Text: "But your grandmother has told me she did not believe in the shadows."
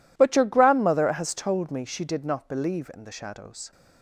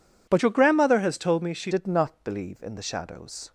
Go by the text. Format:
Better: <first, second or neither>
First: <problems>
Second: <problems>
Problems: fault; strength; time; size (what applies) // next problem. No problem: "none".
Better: first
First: none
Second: changes voice from "your" to "she"; from 0.4 to 1.6 s; 1.2 s long